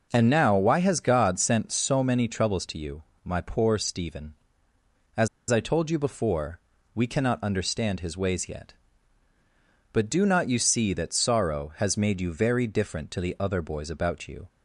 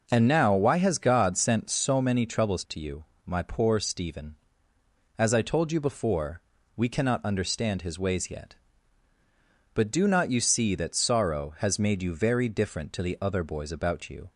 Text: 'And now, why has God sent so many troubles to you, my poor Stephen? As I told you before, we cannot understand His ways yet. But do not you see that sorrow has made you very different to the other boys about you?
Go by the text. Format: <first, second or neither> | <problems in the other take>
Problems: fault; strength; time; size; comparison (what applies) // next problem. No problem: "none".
second | pauses between "As" and "I"; slight; at 5.2 s; 0.22 s long